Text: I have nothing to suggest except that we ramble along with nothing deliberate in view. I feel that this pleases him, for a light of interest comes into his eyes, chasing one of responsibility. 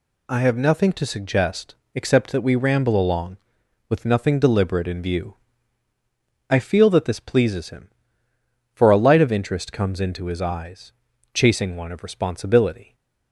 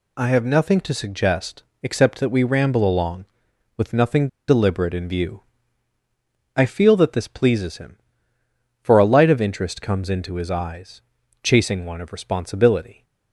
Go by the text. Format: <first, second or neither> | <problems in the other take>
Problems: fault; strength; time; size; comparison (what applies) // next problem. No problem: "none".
first | pauses between "suggest" and "except"; slight; at 1.6 s; 0.18 s long; slight in the first // pauses between "nothing" and "deliberate"; slight; at 4.2 s; 0.20 s long